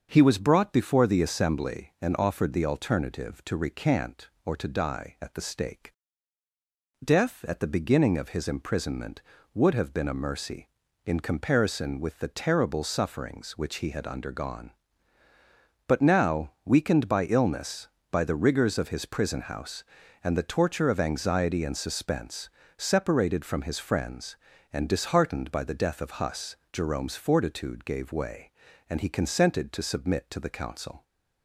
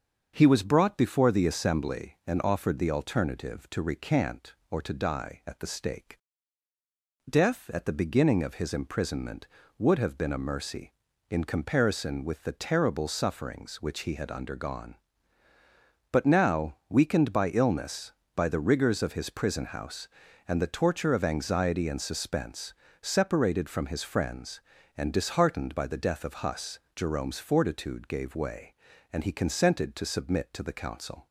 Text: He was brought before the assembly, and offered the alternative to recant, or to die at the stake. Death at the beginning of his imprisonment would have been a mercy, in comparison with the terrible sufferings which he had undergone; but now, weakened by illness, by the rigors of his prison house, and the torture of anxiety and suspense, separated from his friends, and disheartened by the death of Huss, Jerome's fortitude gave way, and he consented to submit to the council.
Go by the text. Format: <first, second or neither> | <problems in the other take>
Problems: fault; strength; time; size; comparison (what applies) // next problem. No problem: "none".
neither | starts louder than the rest; the same in both